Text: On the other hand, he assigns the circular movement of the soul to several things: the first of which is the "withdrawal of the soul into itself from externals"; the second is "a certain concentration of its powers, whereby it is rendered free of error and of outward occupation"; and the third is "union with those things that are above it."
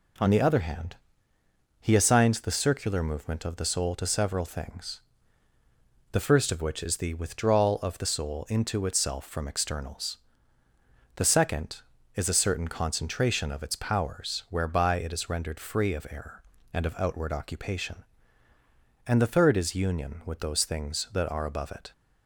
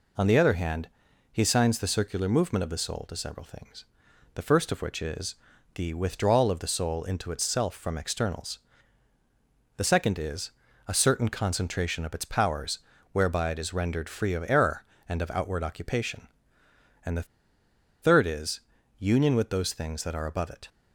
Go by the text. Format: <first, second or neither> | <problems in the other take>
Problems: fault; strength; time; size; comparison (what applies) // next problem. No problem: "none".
first | pauses between "is" and "the"; at 5.3 s; 0.40 s long // pauses between "is" and "a"; slight; at 10.5 s; 0.36 s long // pauses between "the" and "third"; noticeable; at 17.2 s; 0.76 s long // pauses between "is" and "union"; at 18.5 s; 0.40 s long